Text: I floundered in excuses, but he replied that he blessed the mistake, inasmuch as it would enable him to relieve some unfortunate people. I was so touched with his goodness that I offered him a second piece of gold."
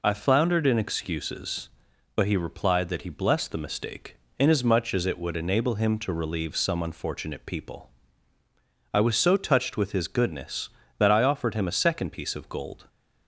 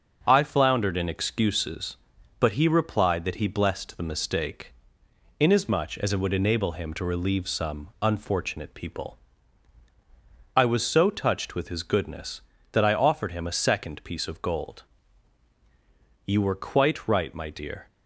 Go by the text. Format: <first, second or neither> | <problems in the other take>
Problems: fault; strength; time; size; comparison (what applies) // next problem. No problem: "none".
first | starts louder than the rest; until 1.2 s; 6.5 dB // goes on to say "You were quite right my dear"; from 16.2 s on; 1.6 s long